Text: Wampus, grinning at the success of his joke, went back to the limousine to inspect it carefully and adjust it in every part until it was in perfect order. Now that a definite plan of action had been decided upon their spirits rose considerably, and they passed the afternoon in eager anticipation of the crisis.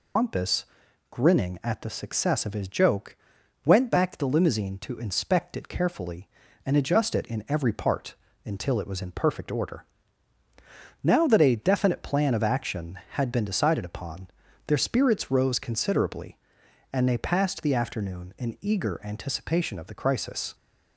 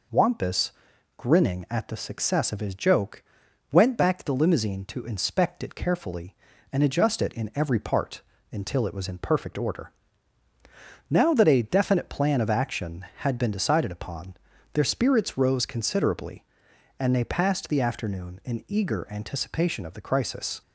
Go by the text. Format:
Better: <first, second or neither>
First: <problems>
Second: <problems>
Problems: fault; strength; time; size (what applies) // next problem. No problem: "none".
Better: second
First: loses the start of "Wampus"; at 0.1 s; 110 ms // pauses between "part" and "until"; slight; at 8.1 s; 0.30 s long // pauses between "upon" and "their"; at 14.2 s; 0.38 s long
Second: pauses between "part" and "until"; slight; at 8.2 s; 0.30 s long // pauses between "upon" and "their"; at 14.3 s; 0.38 s long